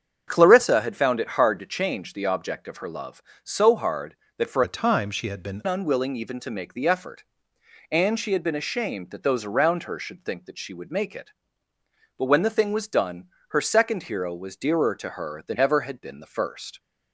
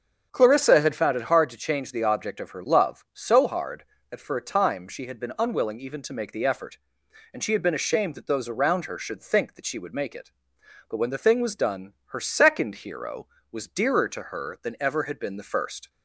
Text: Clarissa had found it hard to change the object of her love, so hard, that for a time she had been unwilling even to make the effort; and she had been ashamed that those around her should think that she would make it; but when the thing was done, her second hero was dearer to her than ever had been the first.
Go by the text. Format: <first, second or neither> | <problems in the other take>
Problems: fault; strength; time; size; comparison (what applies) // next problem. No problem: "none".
second | starts louder than the rest; strong; until 1.2 s; 7.5 dB; strong in the second // changes voice from "a" to "been"; from 4.6 to 5.6 s; 1.0 s long